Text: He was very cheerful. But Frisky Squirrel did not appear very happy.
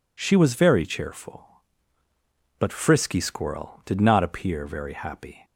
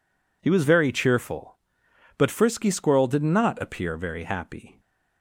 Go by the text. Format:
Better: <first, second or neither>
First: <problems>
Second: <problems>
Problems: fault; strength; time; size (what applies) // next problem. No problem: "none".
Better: second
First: says "She" for "He"; at 0.2 s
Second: none